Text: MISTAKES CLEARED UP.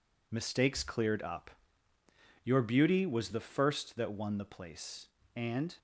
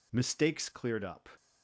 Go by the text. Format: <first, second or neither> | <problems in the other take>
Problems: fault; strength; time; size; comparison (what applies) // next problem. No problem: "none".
second | goes on to say "Your beauty was the first that won the place And"; strong; from 2.4 s on; 3.3 s long